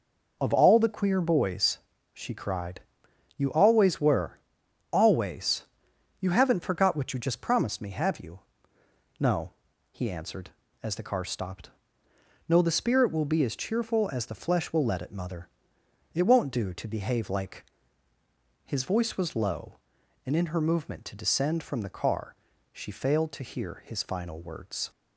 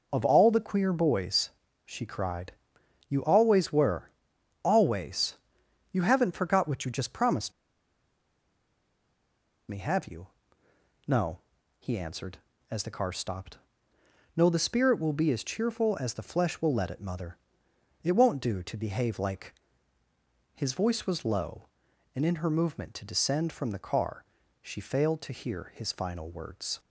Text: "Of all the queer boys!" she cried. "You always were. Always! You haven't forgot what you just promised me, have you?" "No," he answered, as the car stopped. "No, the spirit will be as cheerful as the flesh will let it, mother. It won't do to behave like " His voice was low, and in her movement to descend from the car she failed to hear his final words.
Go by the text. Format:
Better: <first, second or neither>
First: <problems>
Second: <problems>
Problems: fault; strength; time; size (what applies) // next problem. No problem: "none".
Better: first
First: pauses between "car" and "she"; at 22.3 s; 0.40 s long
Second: pauses between "promised" and "me"; strong; at 7.5 s; 2.1 s long // pauses between "car" and "she"; at 24.2 s; 0.40 s long